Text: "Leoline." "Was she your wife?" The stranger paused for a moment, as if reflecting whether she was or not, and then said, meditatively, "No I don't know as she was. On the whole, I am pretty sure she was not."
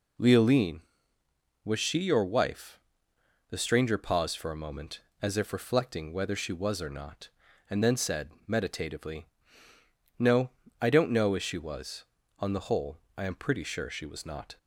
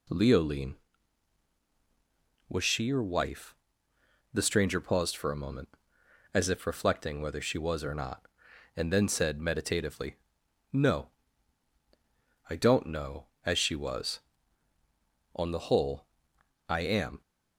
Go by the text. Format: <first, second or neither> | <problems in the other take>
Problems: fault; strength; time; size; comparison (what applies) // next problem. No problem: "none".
first | pauses between "No" and "I"; strong; at 11.1 s; 1.3 s long; slight in the first // stops before "pretty sure she was not"; at 17.2 s